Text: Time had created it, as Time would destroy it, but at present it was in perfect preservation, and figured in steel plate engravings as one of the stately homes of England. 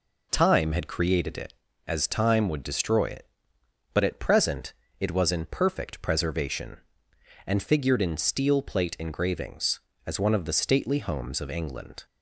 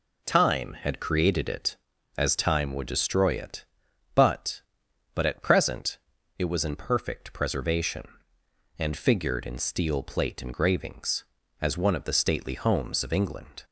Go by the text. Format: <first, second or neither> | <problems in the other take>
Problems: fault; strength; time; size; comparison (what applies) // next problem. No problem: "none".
first | says "but" twice; at 5.1 s // pauses between "present" and "it"; at 5.9 s; 0.40 s long; slight in the first